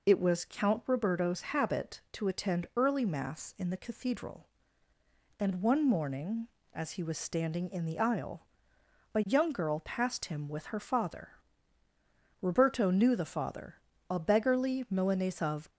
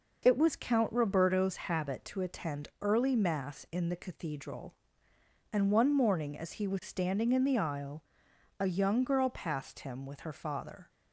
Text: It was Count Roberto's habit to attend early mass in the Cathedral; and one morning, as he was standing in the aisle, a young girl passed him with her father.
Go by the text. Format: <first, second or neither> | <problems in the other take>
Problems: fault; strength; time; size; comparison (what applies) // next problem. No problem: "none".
second | goes on to say "Roberto knew the father a beggarly Milanese of"; strong; from 12.4 s on; 3.2 s long